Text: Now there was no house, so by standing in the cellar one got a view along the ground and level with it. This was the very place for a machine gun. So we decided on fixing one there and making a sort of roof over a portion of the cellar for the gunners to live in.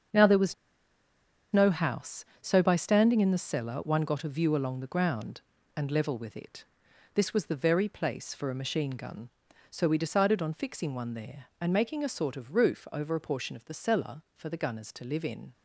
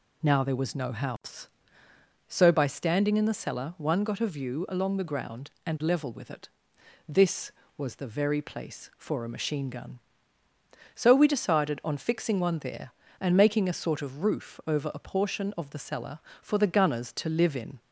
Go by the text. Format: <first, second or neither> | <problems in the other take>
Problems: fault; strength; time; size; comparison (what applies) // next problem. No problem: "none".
second | starts louder than the rest; until 2.1 s; 7 dB // pauses between "was" and "no"; at 0.5 s; 0.98 s long